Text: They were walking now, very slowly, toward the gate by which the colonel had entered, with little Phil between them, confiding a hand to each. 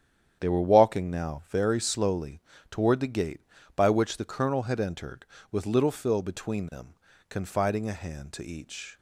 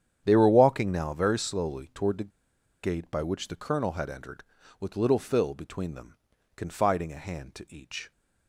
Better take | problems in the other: first | starts louder than the rest; strong; until 1.2 s; 9 dB; strong in the first // pauses between "the" and "gate"; noticeable; at 2.3 s; 0.54 s long

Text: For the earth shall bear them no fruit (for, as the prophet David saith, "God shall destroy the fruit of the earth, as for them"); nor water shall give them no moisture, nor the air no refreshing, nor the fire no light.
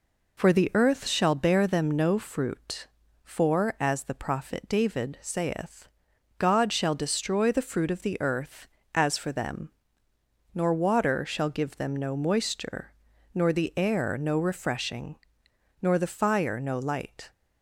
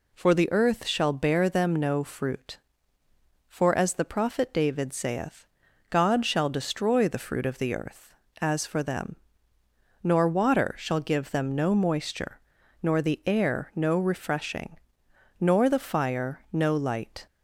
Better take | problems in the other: neither | none

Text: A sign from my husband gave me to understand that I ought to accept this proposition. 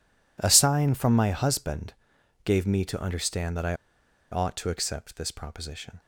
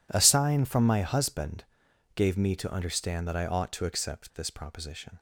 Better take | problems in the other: second | pauses between "husband" and "gave"; noticeable; at 1.9 s; 0.52 s long; noticeable in the second // pauses between "I" and "ought"; noticeable; at 3.7 s; 0.56 s long

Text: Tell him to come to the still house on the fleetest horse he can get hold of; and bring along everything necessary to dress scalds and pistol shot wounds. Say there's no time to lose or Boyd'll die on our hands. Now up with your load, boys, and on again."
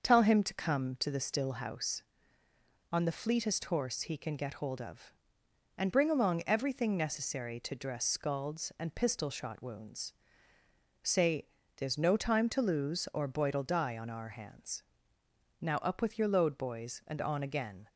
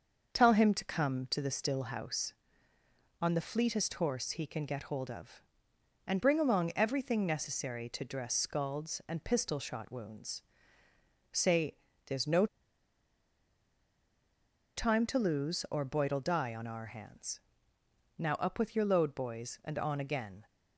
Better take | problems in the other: first | starts louder than the rest; until 1.4 s; 6.5 dB; also in the first // pauses between "Say" and "there's"; slight; at 11.7 s; 0.30 s long; slight in the first // pauses between "no" and "time"; strong; at 12.4 s; 2.3 s long

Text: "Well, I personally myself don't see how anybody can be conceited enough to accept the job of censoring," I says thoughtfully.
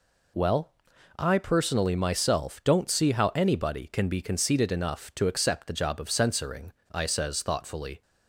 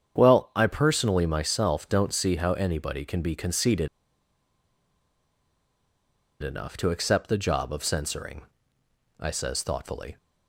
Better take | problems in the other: first | starts louder than the rest; strong; until 1.2 s; 8 dB // pauses between "conceited" and "enough"; strong; at 3.8 s; 2.5 s long

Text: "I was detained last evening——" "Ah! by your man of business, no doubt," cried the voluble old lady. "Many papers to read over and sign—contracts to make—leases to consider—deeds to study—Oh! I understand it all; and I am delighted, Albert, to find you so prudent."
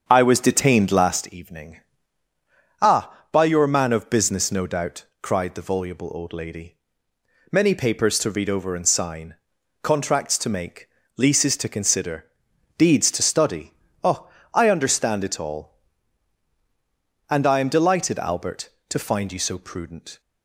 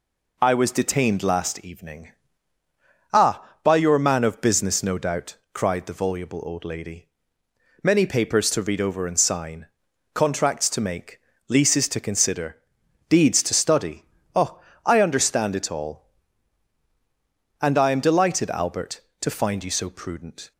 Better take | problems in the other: second | starts louder than the rest; strong; until 1.3 s; 7.5 dB

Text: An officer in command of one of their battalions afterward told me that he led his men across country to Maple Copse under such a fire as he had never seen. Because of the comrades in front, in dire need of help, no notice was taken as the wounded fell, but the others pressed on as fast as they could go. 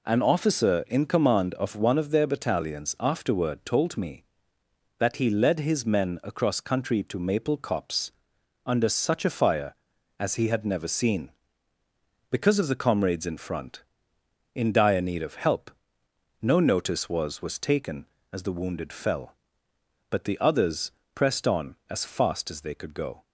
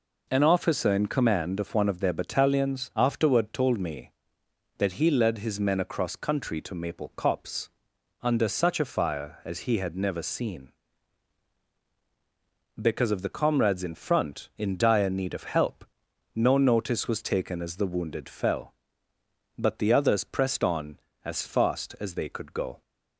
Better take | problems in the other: second | pauses between "Copse" and "under"; noticeable; at 8.1 s; 0.54 s long; noticeable in the second // says "was" twice; at 17.4 s // pauses between "others" and "pressed"; slight; at 20.9 s; 0.22 s long

